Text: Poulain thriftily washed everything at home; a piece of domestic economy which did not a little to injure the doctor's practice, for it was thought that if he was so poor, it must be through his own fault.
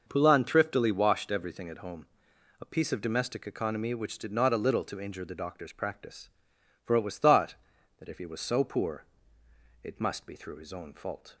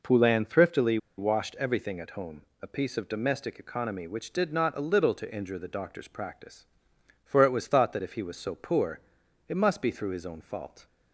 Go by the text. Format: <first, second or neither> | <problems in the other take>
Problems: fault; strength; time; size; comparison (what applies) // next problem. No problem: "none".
first | pauses between "thriftily" and "washed"; slight; at 0.9 s; 0.20 s long